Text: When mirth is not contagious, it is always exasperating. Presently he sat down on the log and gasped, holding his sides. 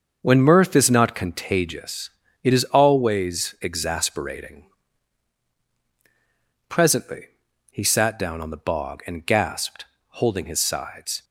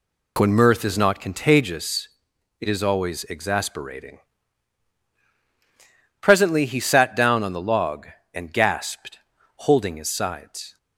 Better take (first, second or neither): second